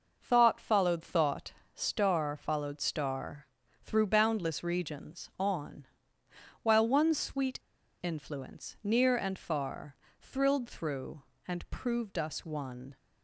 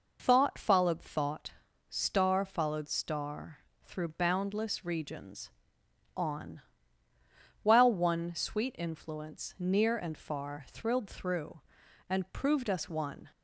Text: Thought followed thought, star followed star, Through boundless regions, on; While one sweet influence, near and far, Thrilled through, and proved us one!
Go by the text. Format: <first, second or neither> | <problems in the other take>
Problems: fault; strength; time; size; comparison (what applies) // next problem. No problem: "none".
second | pauses between "sweet" and "influence"; at 7.6 s; 0.40 s long